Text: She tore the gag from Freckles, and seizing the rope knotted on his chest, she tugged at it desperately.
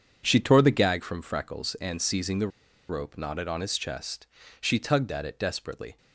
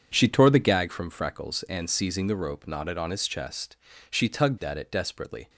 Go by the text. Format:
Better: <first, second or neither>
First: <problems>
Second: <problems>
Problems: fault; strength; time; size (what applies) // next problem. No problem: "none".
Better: second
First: pauses between "the" and "rope"; at 2.4 s; 0.40 s long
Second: none